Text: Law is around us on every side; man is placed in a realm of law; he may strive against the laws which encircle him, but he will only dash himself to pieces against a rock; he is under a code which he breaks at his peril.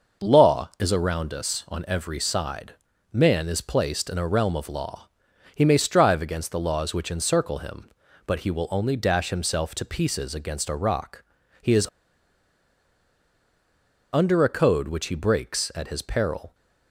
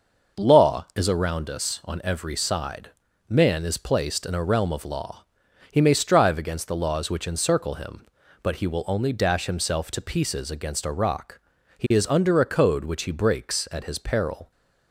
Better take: second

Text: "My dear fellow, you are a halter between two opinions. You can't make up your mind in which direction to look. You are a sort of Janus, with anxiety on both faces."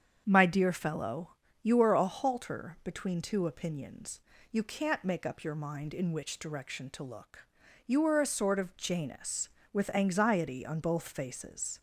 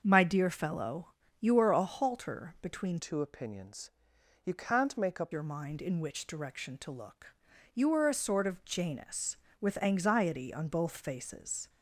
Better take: first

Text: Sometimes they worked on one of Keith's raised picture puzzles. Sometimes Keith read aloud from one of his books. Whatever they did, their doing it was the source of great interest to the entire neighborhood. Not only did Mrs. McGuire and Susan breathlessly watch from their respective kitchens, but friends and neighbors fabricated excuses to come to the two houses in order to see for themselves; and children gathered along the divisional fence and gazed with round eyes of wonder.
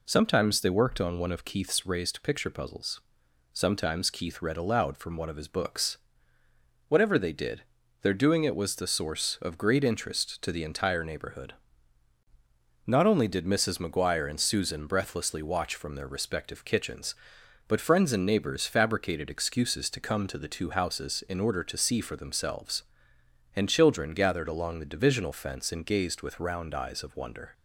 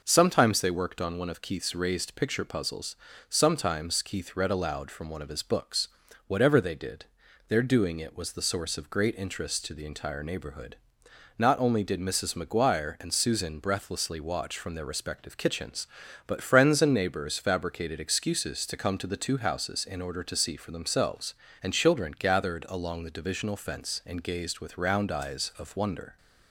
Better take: neither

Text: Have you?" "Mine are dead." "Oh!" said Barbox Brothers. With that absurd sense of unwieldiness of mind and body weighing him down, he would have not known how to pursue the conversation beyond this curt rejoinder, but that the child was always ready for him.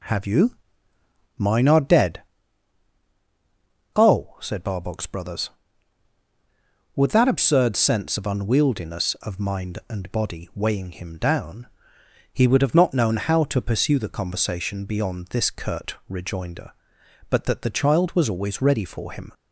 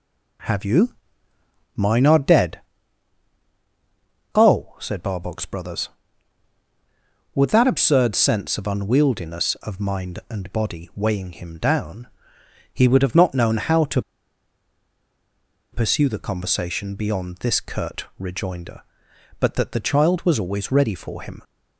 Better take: first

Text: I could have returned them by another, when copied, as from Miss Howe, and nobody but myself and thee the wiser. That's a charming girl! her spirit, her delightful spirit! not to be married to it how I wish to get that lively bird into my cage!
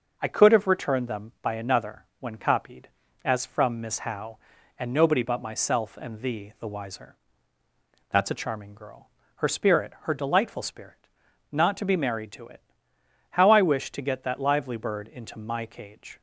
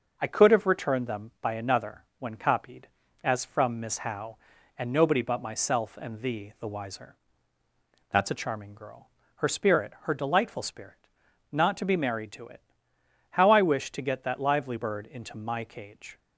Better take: neither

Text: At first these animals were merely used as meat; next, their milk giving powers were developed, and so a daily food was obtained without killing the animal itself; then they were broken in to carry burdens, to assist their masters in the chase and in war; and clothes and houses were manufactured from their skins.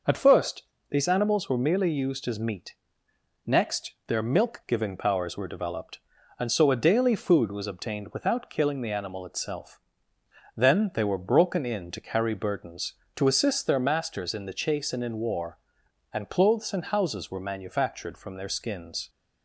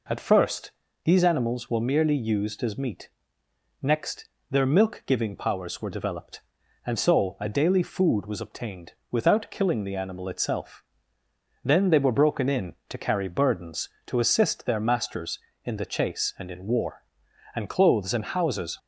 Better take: first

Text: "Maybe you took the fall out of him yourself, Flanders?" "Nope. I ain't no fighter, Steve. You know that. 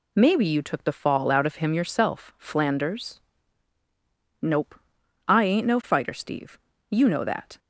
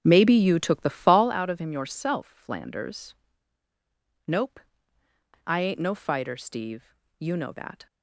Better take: first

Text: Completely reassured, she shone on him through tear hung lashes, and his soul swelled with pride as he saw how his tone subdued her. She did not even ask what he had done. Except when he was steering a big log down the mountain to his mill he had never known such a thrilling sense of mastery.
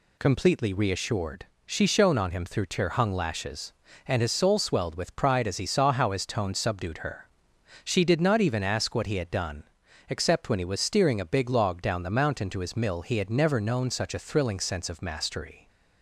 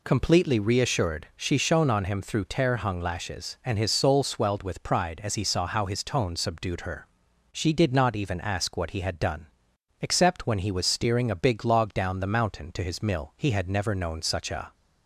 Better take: first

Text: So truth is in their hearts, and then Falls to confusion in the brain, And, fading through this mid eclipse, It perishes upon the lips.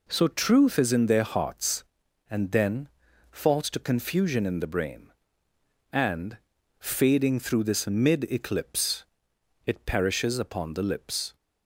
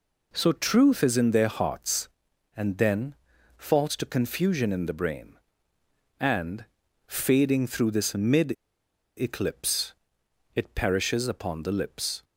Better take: first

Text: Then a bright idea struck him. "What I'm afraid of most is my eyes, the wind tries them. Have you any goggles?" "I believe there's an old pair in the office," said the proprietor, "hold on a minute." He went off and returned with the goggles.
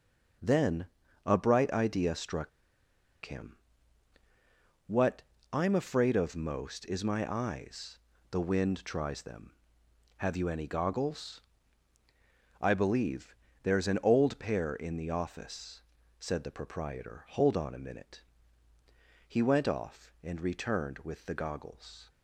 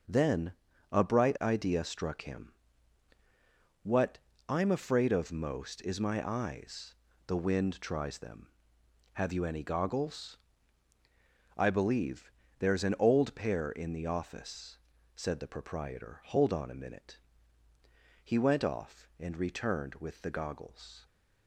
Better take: second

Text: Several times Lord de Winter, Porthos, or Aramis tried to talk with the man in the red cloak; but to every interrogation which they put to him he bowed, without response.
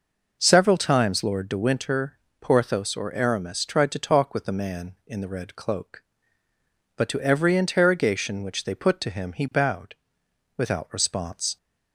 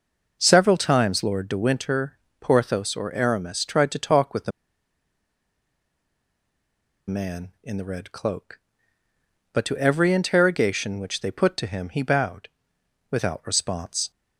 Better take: first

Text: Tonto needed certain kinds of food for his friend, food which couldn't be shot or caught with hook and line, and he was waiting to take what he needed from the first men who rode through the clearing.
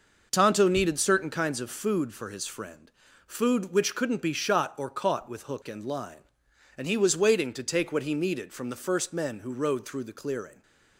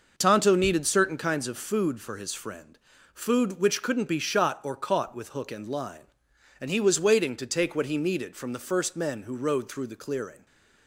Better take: neither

